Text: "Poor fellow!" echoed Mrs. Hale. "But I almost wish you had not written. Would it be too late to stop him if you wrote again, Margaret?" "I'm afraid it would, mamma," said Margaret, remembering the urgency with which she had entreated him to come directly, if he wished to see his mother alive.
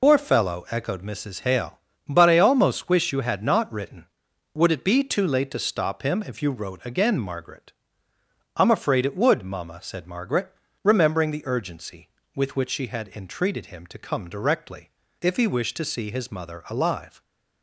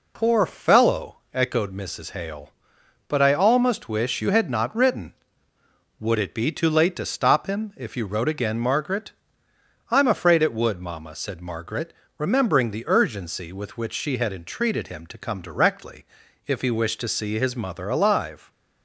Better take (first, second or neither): second